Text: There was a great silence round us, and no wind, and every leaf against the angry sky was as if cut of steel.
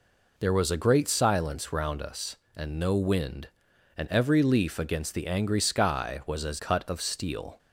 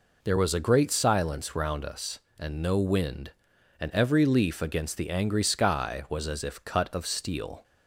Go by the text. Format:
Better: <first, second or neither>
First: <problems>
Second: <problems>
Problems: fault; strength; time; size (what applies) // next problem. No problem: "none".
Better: second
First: skips "if"; at 6.5 s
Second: none